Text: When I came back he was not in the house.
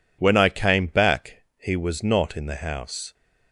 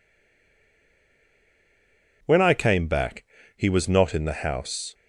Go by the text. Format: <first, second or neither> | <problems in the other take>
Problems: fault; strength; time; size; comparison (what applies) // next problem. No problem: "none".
first | stays silent before the first word; until 2.2 s; 2.2 s long // pauses between "back" and "he"; slight; at 3.2 s; 0.32 s long